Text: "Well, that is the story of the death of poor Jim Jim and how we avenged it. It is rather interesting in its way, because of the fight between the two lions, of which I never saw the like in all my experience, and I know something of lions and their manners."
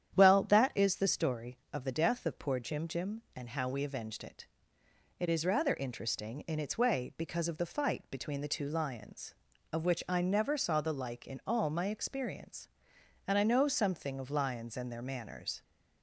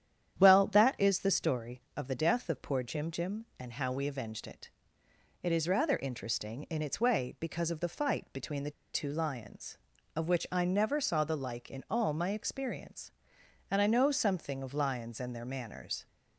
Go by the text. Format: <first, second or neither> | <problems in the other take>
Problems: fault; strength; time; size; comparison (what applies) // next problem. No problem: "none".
first | starts louder than the rest; strong; until 1.4 s; 9.5 dB; strong in the first // pauses between "the" and "two"; slight; at 8.7 s; 0.22 s long